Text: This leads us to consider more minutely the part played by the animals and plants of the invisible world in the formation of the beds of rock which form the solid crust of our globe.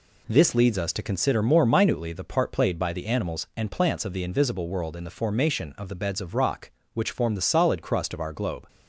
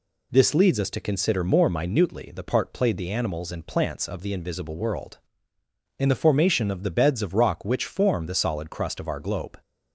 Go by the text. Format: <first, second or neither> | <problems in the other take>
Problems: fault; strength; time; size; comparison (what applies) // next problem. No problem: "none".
first | skips "by"; at 2.9 s